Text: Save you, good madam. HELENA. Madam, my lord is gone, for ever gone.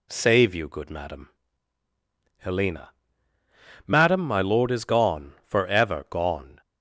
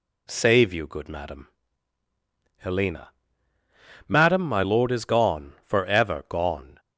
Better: neither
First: none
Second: none

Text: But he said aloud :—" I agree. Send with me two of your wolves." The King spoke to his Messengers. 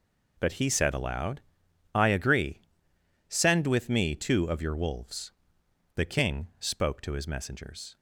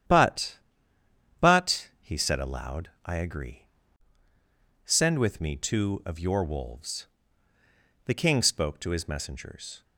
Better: first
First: none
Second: starts louder than the rest; strong; until 2.0 s; 10 dB // says "But" twice; at 1.4 s

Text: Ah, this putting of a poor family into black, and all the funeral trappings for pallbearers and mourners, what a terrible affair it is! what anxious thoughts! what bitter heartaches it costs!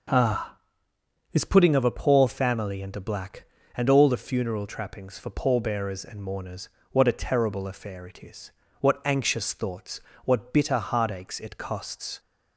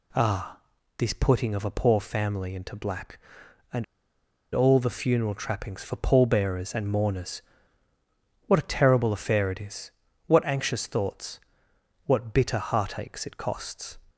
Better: first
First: none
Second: pauses between "and" and "all"; noticeable; at 3.8 s; 0.70 s long

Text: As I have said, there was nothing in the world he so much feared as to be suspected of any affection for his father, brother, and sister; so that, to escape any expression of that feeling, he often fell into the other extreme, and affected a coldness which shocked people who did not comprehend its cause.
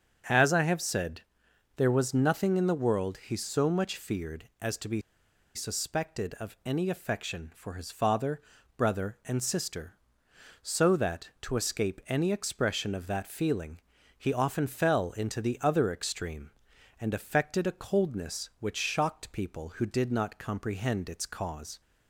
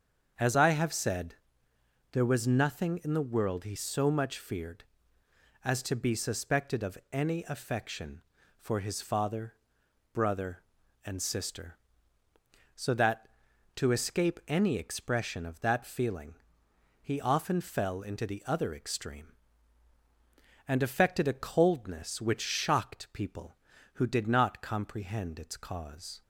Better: second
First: starts louder than the rest; strong; until 1.8 s; 7.5 dB // pauses between "be" and "suspected"; noticeable; at 5.0 s; 0.54 s long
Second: starts louder than the rest; until 2.1 s; 6.5 dB

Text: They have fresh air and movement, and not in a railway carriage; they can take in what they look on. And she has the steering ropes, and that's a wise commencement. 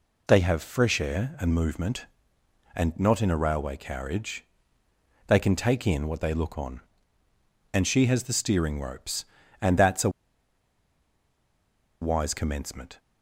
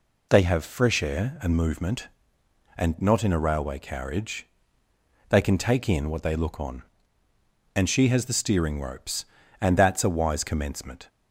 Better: second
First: pauses between "a" and "wise"; strong; at 10.1 s; 1.9 s long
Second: none

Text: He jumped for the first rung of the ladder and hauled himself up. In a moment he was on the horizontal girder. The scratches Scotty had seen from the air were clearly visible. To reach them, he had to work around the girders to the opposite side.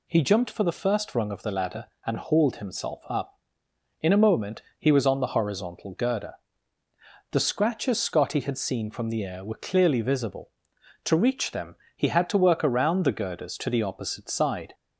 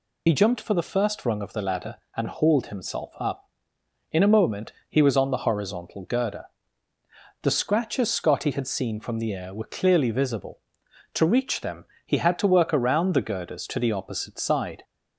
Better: first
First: pauses between "moment" and "he"; slight; at 4.6 s; 0.16 s long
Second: loses the start of "He"; at 0.2 s; 65 ms // pauses between "moment" and "he"; slight; at 4.7 s; 0.16 s long

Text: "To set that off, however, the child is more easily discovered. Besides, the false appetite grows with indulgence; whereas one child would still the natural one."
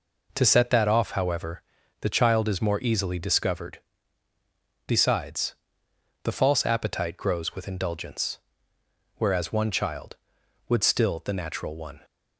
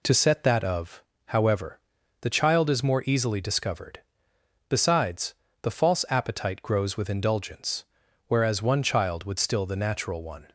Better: first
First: none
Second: says "of" for "off"; at 0.6 s

